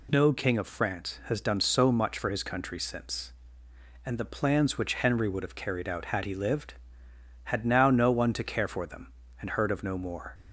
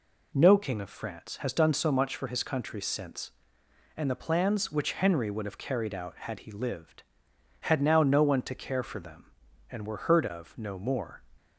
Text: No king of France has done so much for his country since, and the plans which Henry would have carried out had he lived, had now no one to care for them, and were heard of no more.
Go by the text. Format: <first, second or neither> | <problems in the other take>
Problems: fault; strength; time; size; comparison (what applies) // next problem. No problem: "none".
second | skips "were"; at 9.5 s